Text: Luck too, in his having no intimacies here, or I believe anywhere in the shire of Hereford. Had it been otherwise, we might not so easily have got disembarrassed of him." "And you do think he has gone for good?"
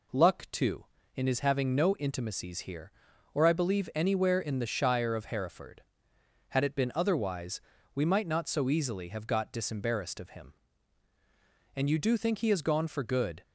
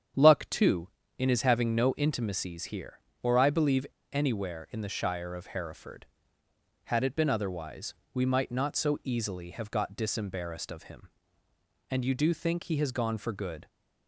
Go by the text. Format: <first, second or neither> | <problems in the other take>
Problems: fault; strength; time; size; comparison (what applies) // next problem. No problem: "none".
first | starts louder than the rest; strong; until 1.4 s; 8.5 dB // pauses between "believe" and "anywhere"; slight; at 3.8 s; 0.27 s long